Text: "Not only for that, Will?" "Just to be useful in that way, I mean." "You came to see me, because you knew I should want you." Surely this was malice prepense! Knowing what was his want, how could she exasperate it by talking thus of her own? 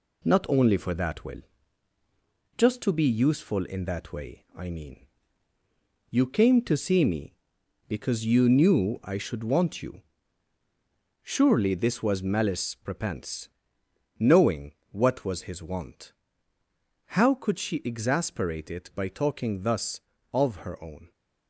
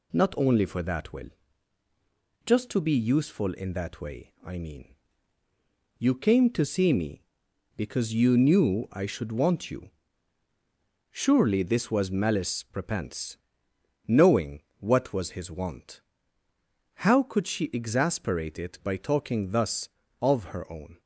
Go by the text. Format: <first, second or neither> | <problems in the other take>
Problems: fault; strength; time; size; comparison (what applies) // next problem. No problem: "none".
second | gets quieter; noticeable; throughout; 4 dB // pauses between "Knowing" and "what"; slight; at 14.7 s; 0.18 s long; slight in the second